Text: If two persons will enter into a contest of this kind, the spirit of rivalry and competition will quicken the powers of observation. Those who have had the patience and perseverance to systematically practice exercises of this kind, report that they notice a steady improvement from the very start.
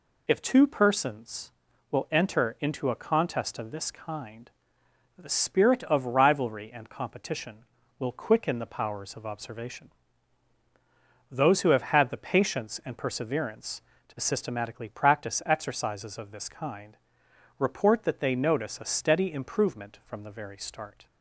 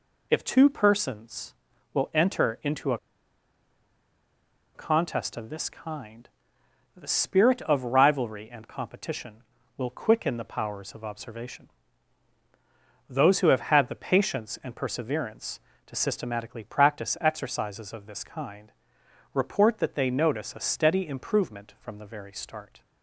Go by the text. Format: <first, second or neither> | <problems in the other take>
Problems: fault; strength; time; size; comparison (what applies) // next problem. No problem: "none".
first | pauses between "a" and "contest"; strong; at 2.9 s; 1.7 s long